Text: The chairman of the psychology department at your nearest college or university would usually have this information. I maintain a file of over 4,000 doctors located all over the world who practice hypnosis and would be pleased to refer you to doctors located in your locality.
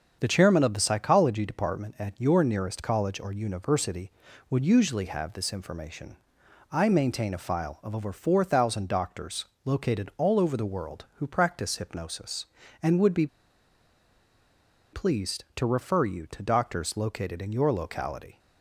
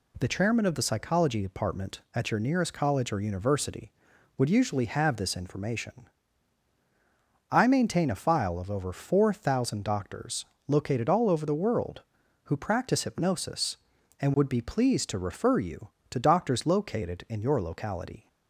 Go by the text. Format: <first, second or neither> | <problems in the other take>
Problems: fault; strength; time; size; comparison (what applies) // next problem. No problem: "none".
second | starts louder than the rest; until 1.2 s; 7 dB // pauses between "doctors" and "located"; slight; at 9.4 s; 0.20 s long; slight in the second // pauses between "be" and "pleased"; strong; at 13.2 s; 1.6 s long